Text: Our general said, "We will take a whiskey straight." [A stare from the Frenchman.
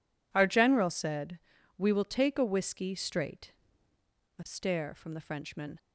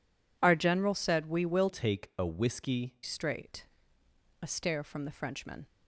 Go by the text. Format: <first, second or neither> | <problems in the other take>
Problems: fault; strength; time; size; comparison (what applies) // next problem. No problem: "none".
first | changes voice from "take" to "whiskey"; from 1.6 to 2.9 s; 1.3 s long